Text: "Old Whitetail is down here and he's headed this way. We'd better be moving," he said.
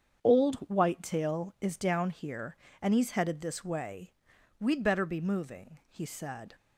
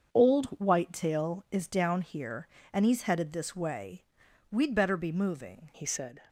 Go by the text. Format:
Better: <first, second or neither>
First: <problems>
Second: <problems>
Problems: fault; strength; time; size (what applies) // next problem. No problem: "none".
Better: first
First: starts louder than the rest; strong; until 1.2 s; 7.5 dB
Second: starts louder than the rest; until 1.1 s; 7 dB // changes voice at "he"; from 5.7 s on; 0.5 s long